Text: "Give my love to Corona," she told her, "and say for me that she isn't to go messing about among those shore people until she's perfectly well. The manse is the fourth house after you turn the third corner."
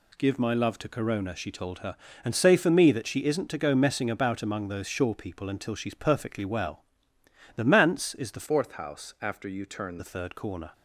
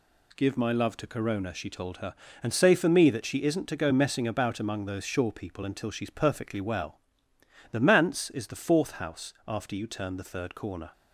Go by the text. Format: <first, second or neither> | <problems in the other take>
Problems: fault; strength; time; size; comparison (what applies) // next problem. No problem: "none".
second | changes voice from "fourth" to "turn"; from 8.4 to 9.9 s; 1.5 s long